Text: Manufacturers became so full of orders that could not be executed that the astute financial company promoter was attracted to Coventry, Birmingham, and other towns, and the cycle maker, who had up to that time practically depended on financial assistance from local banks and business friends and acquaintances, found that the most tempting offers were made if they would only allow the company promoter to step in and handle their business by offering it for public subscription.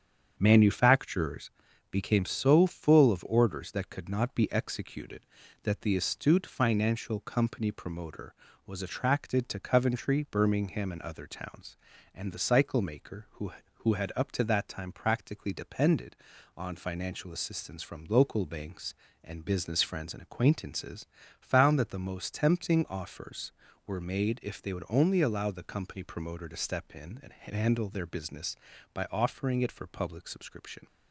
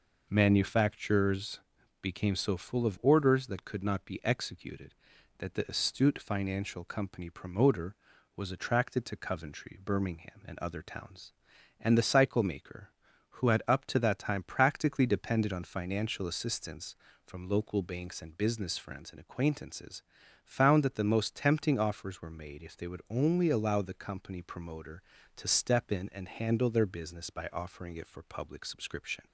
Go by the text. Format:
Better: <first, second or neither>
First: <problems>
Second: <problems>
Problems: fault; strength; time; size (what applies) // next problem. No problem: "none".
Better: second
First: starts louder than the rest; strong; until 1.3 s; 8 dB // pauses between "Manufacturers" and "became"; at 1.5 s; 0.40 s long // says "who" twice; at 13.8 s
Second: pauses between "Manufacturers" and "became"; at 1.5 s; 0.42 s long